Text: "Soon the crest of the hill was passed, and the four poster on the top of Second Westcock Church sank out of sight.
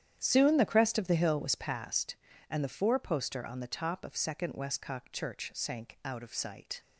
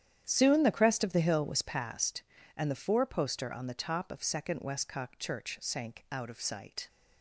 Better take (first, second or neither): neither